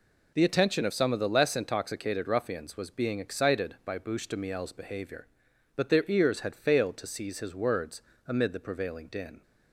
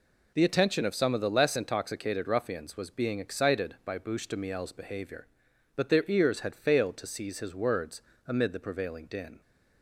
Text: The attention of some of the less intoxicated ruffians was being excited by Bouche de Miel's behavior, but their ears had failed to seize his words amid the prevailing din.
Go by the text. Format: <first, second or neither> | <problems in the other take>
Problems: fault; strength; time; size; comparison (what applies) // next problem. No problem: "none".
neither | pauses between "words" and "amid"; slight; the same in both